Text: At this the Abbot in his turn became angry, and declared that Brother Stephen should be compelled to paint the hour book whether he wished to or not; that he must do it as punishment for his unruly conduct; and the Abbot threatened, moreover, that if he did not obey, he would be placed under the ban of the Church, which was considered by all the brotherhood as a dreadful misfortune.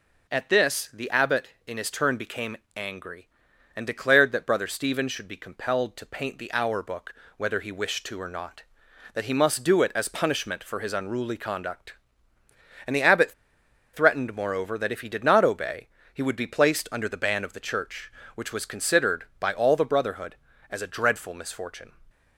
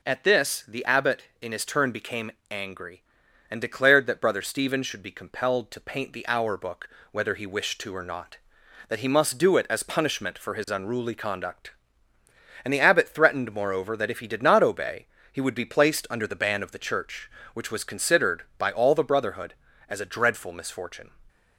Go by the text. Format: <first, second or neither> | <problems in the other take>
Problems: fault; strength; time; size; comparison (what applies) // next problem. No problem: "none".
second | pauses between "became" and "angry"; slight; at 2.5 s; 0.18 s long; slight in the second // pauses between "book" and "whether"; slight; at 7.1 s; 0.24 s long; slight in the second // pauses between "Abbot" and "threatened"; noticeable; at 13.3 s; 0.62 s long